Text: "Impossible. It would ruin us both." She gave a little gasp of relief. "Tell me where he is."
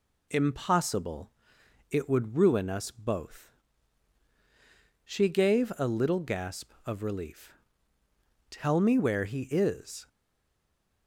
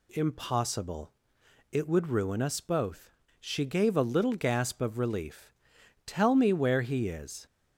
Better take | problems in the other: second | stays silent after the last word; from 10.0 s on; 1.0 s long

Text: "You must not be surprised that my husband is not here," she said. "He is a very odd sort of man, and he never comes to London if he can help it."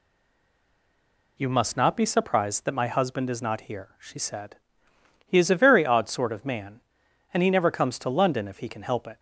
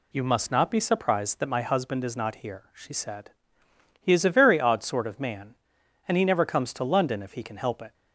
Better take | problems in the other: second | stays silent before the first word; noticeable; until 1.3 s; 1.3 s long

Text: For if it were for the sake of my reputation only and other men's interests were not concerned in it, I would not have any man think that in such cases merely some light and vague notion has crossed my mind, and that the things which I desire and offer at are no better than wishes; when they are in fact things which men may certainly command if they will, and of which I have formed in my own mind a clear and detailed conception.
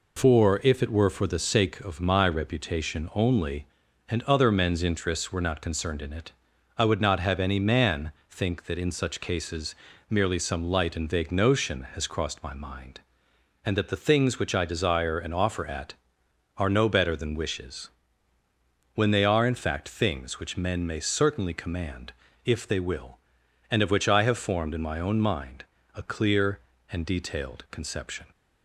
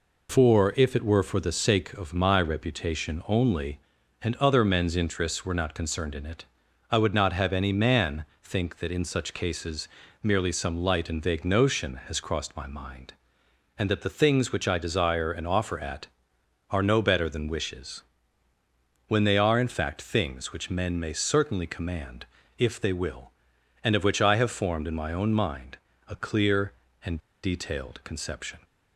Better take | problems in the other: first | pauses between "man" and "think"; slight; at 8.2 s; 0.18 s long; slight in the first // pauses between "cases" and "merely"; slight; at 9.8 s; 0.34 s long; slight in the first // pauses between "command" and "if"; slight; at 22.2 s; 0.32 s long; slight in the first // pauses between "mind" and "a"; slight; at 25.7 s; 0.30 s long; slight in the first // pauses between "and" and "detailed"; slight; at 27.1 s; 0.24 s long

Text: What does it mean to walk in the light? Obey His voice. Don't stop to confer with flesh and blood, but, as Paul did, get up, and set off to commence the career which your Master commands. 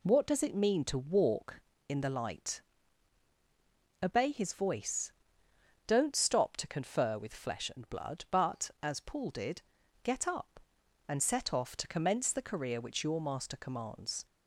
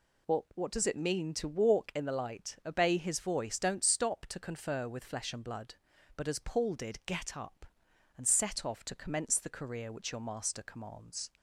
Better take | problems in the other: first | says "What" twice; at 0.5 s

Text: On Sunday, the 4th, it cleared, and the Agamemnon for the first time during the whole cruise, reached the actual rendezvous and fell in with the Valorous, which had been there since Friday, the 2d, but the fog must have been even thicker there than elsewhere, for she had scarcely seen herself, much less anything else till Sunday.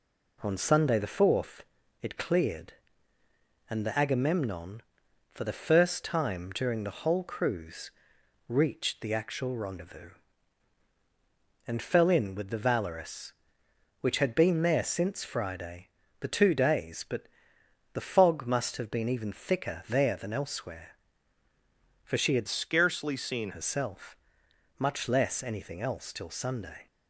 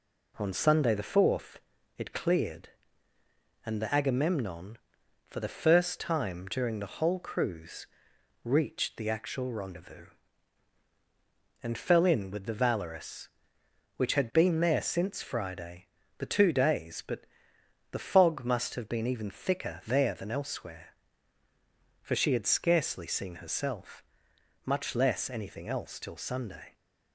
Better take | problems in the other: second | pauses between "but" and "the"; noticeable; at 17.2 s; 0.68 s long; noticeable in the second // changes voice from "scarcely" to "seen"; from 22.4 to 23.4 s; 1.0 s long

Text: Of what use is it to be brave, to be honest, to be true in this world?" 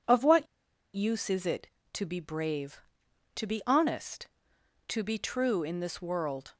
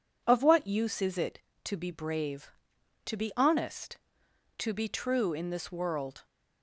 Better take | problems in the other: second | pauses between "what" and "use"; noticeable; at 0.4 s; 0.48 s long

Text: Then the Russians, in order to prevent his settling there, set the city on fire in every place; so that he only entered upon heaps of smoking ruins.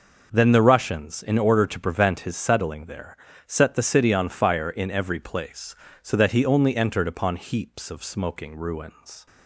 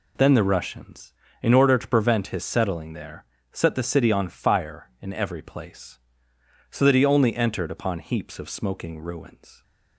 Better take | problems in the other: neither | none

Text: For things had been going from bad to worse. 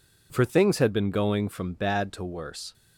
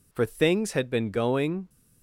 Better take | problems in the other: first | stops before "from bad to worse"; at 1.6 s

